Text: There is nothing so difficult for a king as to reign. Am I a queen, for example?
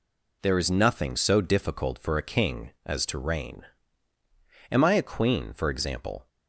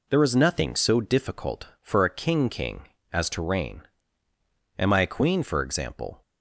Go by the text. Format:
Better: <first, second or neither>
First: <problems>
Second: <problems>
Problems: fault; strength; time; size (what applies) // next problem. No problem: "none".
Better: first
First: none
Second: says "king" twice; at 2.4 s